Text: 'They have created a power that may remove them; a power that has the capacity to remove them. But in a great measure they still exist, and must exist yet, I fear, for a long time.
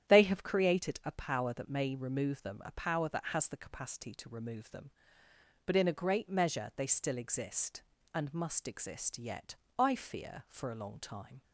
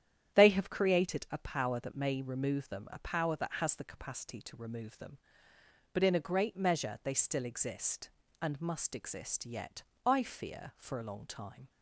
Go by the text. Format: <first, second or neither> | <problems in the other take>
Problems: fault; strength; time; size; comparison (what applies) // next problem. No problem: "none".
neither | starts louder than the rest; strong; the same in both